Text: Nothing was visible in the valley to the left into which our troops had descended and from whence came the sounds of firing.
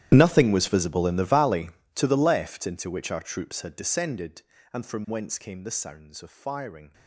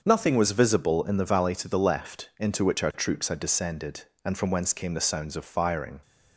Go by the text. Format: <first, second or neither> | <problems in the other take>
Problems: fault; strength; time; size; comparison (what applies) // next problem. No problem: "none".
second | gets quieter; strong; throughout; 20 dB // starts louder than the rest; strong; until 1.1 s; 12 dB; also in the second